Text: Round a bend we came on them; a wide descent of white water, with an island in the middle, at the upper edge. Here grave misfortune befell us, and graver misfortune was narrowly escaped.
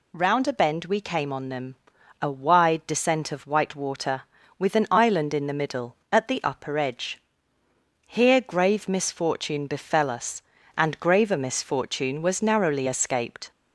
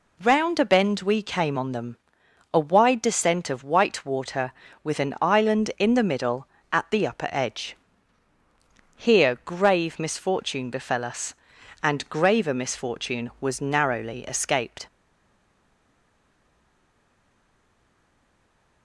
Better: first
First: none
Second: stays silent after the last word; strong; from 14.8 s on; 4.0 s long

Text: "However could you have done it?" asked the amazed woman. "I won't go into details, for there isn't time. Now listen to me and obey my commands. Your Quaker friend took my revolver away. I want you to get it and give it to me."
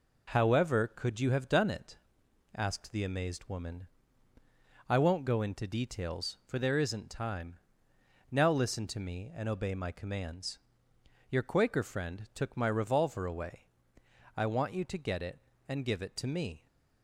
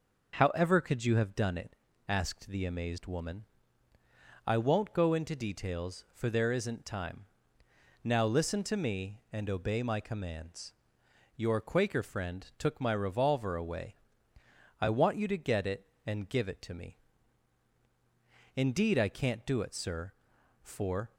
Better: first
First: none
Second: goes on to say "Indeed I can't do it sir for"; strong; from 18.5 s on; 2.5 s long

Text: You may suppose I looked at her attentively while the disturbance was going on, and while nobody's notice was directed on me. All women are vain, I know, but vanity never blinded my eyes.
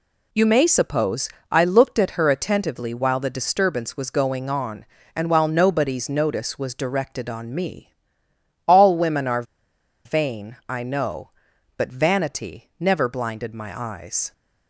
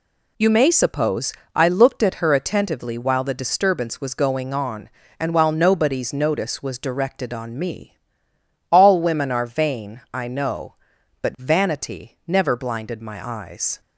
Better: second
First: pauses between "suppose" and "I"; slight; at 1.2 s; 0.22 s long // pauses between "are" and "vain"; noticeable; at 9.4 s; 0.62 s long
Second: pauses between "suppose" and "I"; slight; at 1.3 s; 0.22 s long

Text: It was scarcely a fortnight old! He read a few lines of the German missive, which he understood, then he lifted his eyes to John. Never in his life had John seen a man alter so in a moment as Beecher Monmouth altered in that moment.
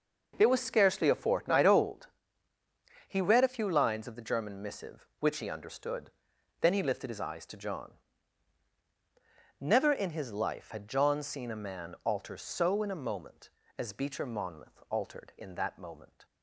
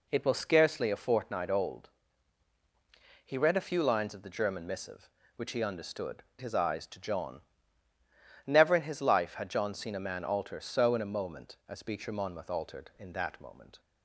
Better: first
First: none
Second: skips "then he lifted"; at 6.3 s

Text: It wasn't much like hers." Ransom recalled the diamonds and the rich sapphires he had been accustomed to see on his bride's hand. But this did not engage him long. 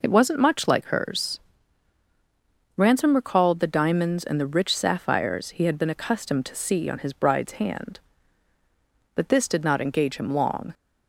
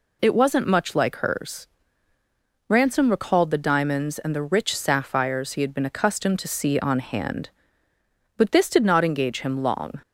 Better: first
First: none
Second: skips "his bride's"; at 6.9 s

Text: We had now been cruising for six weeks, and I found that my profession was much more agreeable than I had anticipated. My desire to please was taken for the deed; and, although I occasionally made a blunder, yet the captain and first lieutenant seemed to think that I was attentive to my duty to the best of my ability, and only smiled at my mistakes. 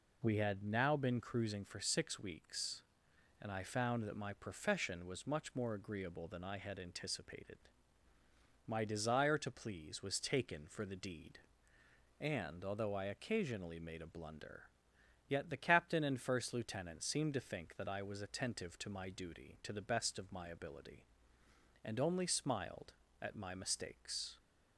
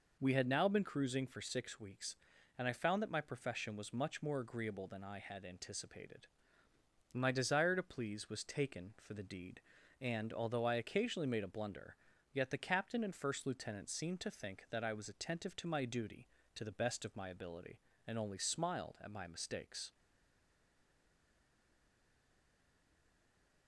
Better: first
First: none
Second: stays silent after the last word; strong; from 19.9 s on; 3.7 s long

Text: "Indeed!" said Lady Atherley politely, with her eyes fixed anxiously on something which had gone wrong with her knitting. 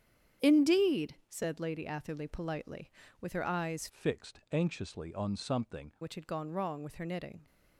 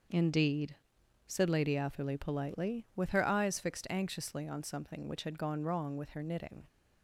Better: second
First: starts louder than the rest; strong; until 1.5 s; 9 dB // changes voice from "fixed" to "something"; from 3.8 to 5.9 s; 2.1 s long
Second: starts louder than the rest; until 1.6 s; 6.5 dB

